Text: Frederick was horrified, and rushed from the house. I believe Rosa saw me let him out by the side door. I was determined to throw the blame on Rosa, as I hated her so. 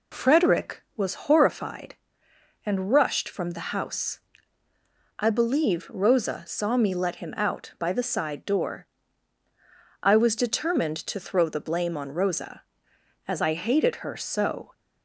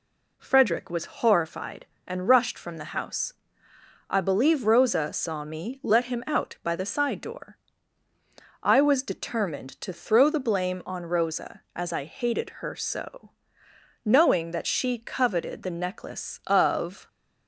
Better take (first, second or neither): first